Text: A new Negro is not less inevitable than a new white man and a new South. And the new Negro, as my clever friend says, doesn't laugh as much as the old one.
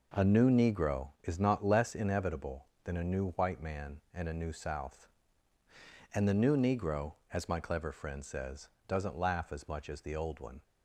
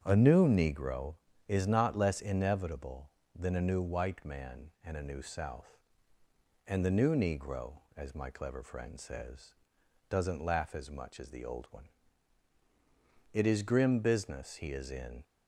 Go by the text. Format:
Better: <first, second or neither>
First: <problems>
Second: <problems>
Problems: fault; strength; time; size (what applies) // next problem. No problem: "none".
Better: first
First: none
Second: starts louder than the rest; strong; until 1.0 s; 8 dB // goes on to say "It is grim business he is in"; strong; from 13.3 s on; 1.9 s long